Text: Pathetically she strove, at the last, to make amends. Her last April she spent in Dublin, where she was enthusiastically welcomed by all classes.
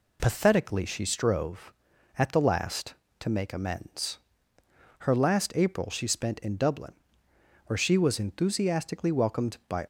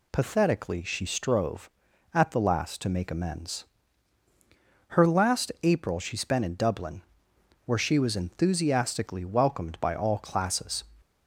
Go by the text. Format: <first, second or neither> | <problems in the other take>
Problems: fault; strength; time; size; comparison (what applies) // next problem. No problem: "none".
second | stops before "all classes"; at 9.8 s